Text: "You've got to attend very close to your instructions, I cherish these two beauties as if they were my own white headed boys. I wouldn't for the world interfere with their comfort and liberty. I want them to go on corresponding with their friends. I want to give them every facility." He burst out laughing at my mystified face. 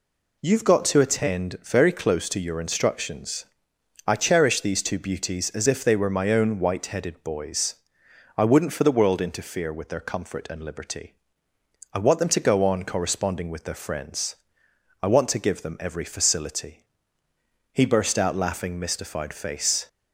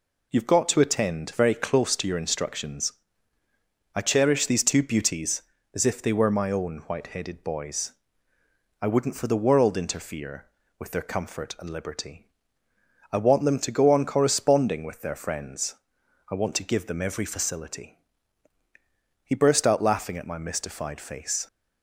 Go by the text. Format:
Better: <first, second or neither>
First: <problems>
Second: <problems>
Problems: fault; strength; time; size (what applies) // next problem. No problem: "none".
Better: second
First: skips "at my"; at 18.7 s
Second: none